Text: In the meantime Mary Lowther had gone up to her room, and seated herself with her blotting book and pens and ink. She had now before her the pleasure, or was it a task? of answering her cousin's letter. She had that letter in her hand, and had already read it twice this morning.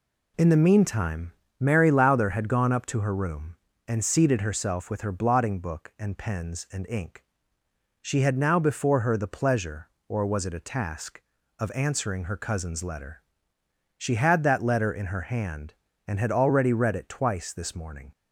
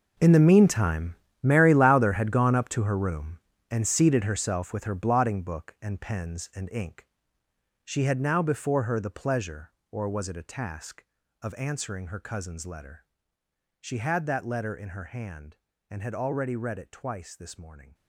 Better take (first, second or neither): first